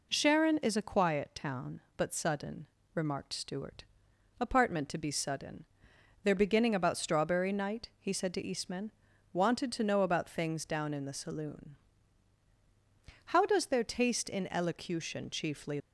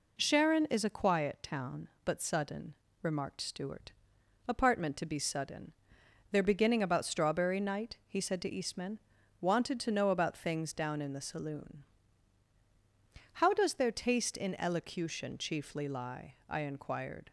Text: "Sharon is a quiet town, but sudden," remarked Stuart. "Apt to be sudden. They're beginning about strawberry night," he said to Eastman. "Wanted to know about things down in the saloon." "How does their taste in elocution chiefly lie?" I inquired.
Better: second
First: stops before "lie I inquired"; at 15.7 s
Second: none

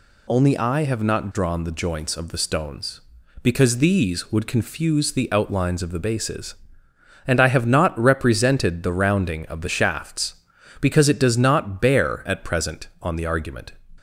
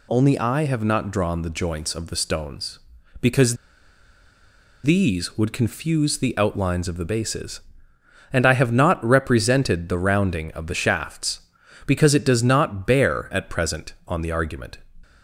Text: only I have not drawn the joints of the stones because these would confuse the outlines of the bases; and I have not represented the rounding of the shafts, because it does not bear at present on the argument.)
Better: first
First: none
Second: pauses between "because" and "these"; strong; at 3.5 s; 1.2 s long

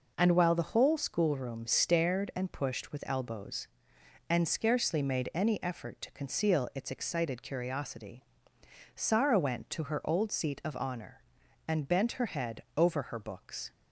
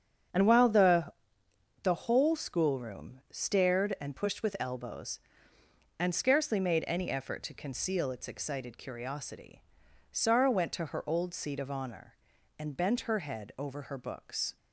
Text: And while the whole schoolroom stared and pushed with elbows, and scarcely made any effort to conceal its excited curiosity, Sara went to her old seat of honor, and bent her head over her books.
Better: first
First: none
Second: starts louder than the rest; strong; until 2.0 s; 7.5 dB // says "the" twice; at 1.8 s

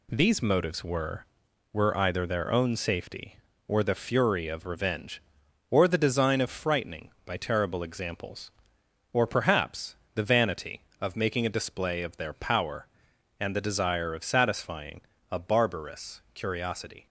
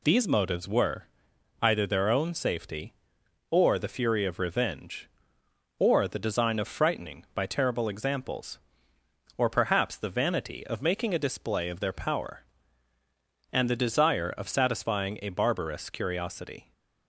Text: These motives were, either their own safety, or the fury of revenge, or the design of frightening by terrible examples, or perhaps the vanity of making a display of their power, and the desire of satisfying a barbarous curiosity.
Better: second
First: says "were" twice; at 1.7 s // pauses between "perhaps" and "the"; slight; at 9.9 s; 0.22 s long // pauses between "satisfying" and "a"; slight; at 15.0 s; 0.28 s long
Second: none

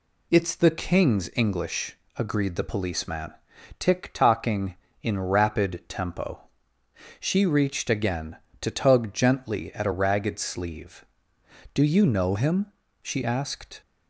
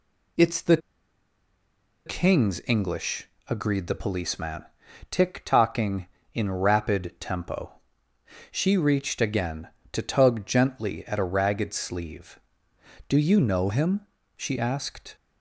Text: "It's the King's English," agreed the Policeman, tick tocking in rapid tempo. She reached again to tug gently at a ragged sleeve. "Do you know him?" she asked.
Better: first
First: none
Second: pauses between "the" and "King's"; strong; at 0.7 s; 1.2 s long

